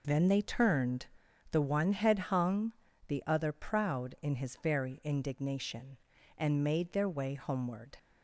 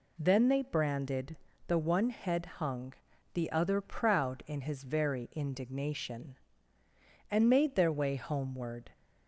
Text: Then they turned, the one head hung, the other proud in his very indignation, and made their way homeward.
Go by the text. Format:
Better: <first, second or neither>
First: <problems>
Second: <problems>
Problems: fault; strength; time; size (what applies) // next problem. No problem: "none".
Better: first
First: none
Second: says "branded" for "turned"; at 0.6 s